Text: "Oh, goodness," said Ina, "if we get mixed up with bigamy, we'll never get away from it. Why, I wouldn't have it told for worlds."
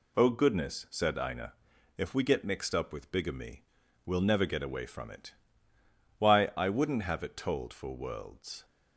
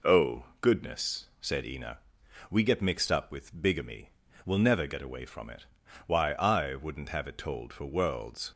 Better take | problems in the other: first | skips "if"; at 2.2 s

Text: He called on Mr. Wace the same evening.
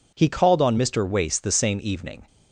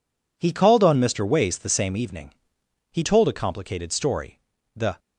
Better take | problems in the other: first | goes on to say "He told a complicated story The"; strong; from 2.9 s on; 2.0 s long

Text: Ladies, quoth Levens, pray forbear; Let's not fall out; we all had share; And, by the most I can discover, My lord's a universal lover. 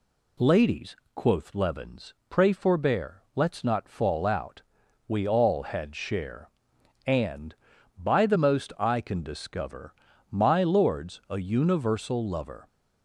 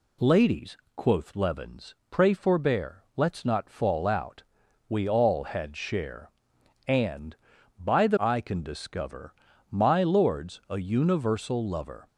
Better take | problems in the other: first | skips "most"; at 8.1 s

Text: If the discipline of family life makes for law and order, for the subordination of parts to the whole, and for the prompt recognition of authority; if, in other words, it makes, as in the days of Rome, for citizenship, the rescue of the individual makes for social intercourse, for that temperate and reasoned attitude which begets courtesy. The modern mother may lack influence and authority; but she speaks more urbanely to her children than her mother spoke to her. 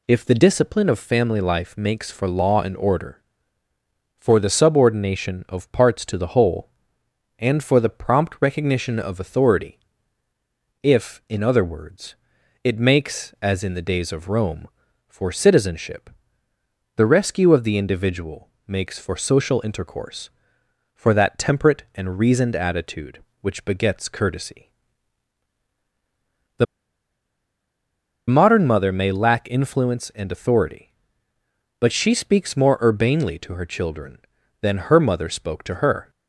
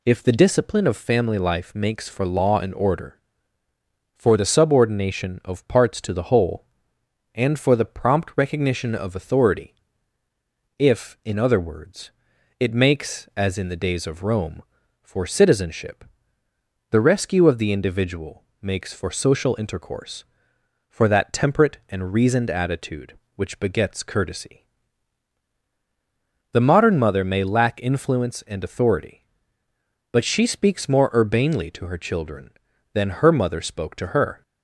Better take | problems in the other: second | pauses between "individual" and "makes"; slight; at 18.4 s; 0.18 s long; slight in the second // pauses between "The" and "modern"; strong; at 26.6 s; 1.6 s long

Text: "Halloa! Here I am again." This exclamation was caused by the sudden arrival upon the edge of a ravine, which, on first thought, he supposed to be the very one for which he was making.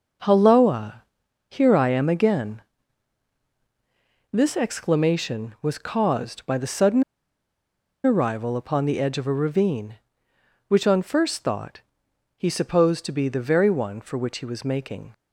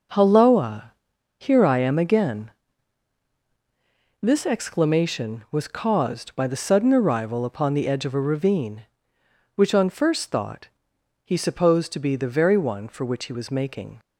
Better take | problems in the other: second | pauses between "sudden" and "arrival"; at 7.0 s; 1.0 s long

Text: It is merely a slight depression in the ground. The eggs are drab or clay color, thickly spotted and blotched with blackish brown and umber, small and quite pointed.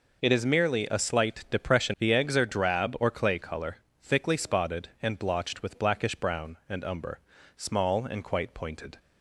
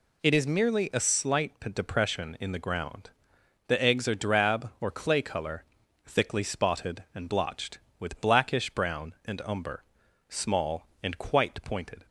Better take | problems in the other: second | skips "in the ground"; at 1.9 s

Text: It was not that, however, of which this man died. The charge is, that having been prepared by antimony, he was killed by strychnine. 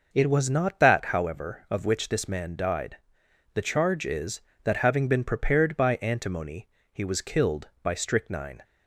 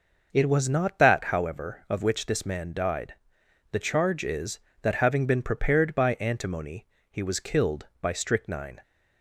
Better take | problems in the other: neither | none

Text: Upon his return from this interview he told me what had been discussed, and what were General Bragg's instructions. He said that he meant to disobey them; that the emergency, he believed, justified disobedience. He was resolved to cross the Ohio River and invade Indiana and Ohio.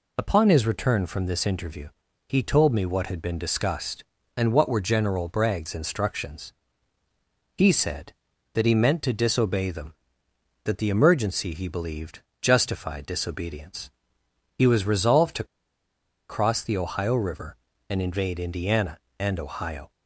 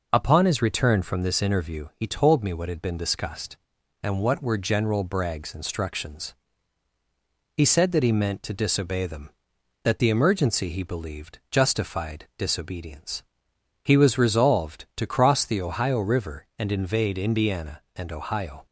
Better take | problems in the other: second | pauses between "interview" and "he"; at 1.8 s; 0.40 s long // pauses between "to" and "cross"; noticeable; at 15.4 s; 0.84 s long

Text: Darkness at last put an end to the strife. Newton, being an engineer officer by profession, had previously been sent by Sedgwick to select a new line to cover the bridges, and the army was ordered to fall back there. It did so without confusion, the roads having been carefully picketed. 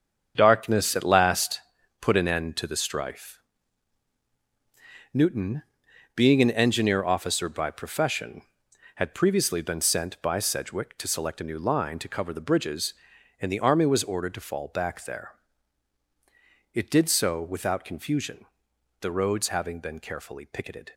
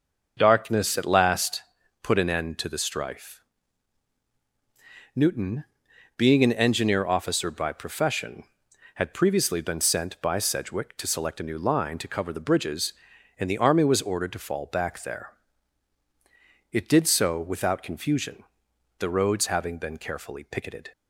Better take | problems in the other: second | gets quieter; strong; throughout; 9 dB // starts louder than the rest; strong; until 1.3 s; 7.5 dB; also in the second // pauses between "last" and "put"; at 1.6 s; 0.40 s long; also in the second

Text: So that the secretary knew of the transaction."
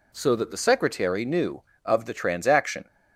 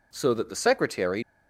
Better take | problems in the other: first | stops before "knew of the transaction"; at 1.2 s

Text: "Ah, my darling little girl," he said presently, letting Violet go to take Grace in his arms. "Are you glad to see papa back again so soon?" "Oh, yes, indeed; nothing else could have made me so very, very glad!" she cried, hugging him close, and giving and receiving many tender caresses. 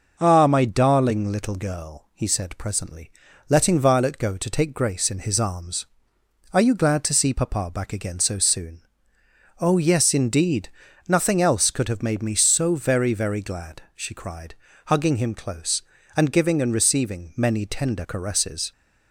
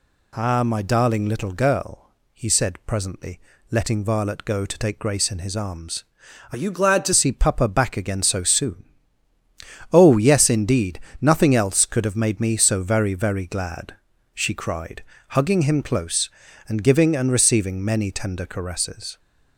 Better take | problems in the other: first | changes voice from "you" to "to"; from 6.5 to 7.1 s; 0.6 s long

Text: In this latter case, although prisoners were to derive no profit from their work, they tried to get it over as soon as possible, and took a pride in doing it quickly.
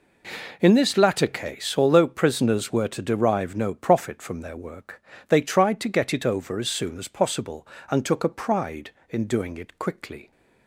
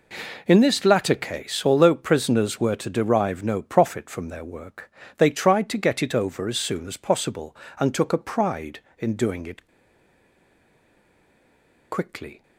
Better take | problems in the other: first | pauses between "it" and "quickly"; strong; at 9.6 s; 2.2 s long

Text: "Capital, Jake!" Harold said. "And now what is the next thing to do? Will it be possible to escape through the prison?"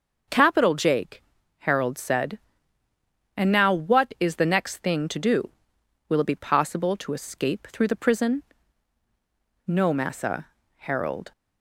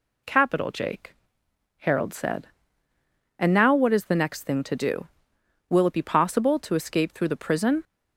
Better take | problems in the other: second | goes on to say "No Massa Harold"; from 9.6 s on; 1.6 s long

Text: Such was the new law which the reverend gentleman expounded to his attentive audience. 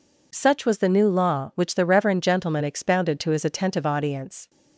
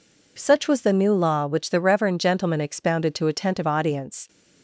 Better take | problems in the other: first | skips "his"; at 3.2 s

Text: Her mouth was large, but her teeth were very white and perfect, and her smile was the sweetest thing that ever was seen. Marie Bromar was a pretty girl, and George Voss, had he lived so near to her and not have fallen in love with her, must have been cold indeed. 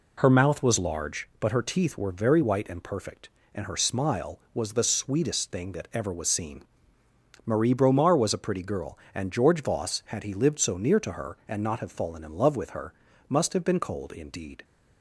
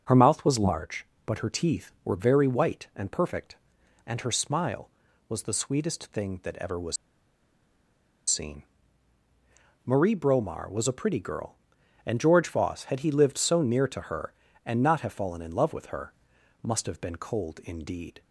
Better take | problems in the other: first | starts louder than the rest; until 1.2 s; 6 dB // pauses between "was" and "seen"; strong; at 6.9 s; 1.3 s long

